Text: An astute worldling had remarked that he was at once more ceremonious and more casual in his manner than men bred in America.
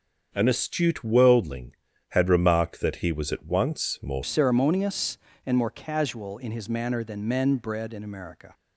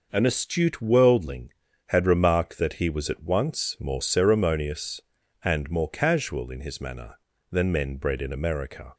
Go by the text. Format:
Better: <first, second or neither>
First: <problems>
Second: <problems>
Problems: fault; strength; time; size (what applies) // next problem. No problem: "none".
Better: second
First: starts louder than the rest; until 1.3 s; 7 dB // changes voice at "ceremonious"; from 4.2 s on; 4.3 s long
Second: none